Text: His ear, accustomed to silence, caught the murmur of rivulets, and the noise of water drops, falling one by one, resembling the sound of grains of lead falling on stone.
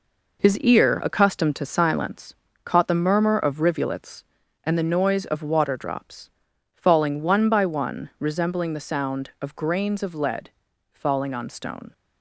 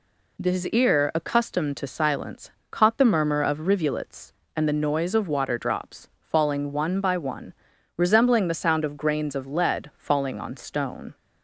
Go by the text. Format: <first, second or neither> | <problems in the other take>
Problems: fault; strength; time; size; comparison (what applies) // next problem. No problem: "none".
second | gets quieter; throughout; 7 dB // pauses between "lead" and "falling"; at 10.4 s; 0.44 s long